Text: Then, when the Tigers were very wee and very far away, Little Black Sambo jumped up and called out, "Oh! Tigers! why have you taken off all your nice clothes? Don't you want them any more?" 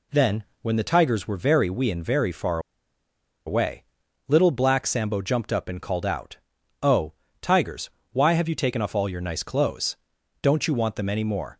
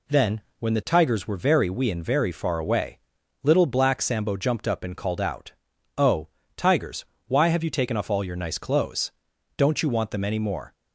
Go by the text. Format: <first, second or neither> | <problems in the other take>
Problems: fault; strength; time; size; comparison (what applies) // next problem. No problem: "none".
second | pauses between "far" and "away"; noticeable; at 2.5 s; 0.87 s long